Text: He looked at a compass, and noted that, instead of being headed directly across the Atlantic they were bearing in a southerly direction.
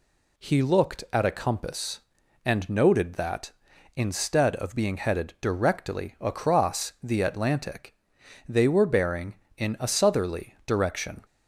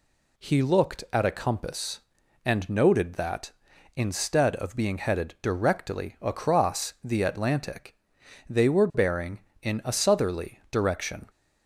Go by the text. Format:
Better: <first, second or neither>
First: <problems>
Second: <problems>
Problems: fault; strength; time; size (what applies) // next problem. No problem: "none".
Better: neither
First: pauses between "Atlantic" and "they"; noticeable; at 7.9 s; 0.56 s long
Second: pauses between "Atlantic" and "they"; noticeable; at 7.9 s; 0.56 s long